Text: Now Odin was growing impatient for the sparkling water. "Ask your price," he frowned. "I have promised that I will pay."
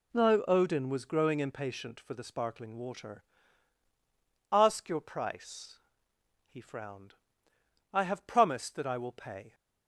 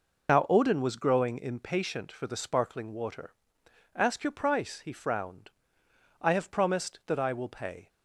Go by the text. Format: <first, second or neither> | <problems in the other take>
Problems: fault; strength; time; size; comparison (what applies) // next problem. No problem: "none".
first | loses the start of "Now"; at 0.2 s; 75 ms